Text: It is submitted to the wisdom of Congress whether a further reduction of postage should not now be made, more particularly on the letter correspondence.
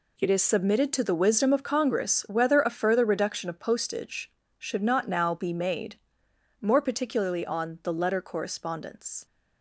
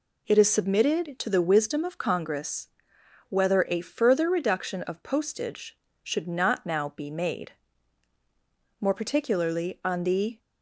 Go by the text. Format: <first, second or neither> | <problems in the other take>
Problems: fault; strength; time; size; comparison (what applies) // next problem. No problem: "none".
first | pauses between "Congress" and "whether"; noticeable; at 2.6 s; 0.62 s long // stops before "letter correspondence"; at 10.3 s